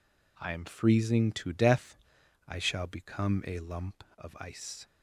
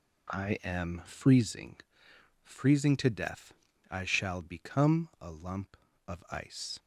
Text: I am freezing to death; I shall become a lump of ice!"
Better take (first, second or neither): first